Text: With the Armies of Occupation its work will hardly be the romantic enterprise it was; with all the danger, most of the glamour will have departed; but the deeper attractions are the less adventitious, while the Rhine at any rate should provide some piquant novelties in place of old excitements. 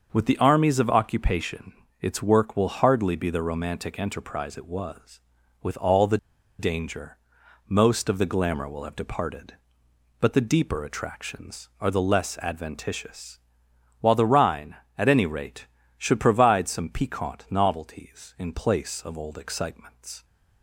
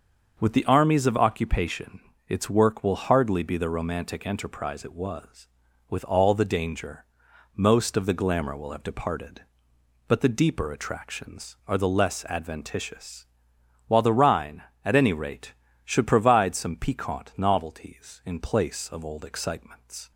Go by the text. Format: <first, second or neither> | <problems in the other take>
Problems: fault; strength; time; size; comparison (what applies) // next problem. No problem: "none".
second | starts louder than the rest; until 1.1 s; 6.5 dB; also in the second // pauses between "Occupation" and "its"; slight; at 1.7 s; 0.28 s long; slight in the second // pauses between "the" and "danger"; at 6.1 s; 0.42 s long